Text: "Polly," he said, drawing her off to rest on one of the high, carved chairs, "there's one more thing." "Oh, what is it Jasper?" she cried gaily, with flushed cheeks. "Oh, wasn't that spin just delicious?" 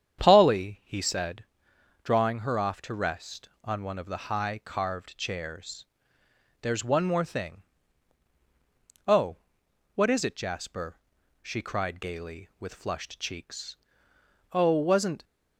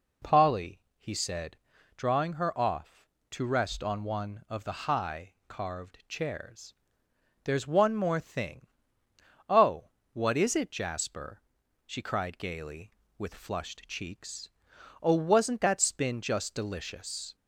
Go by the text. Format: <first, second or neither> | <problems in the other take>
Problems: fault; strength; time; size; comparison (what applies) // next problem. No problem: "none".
second | starts louder than the rest; strong; until 1.2 s; 8.5 dB // stops before "that spin just delicious"; at 15.2 s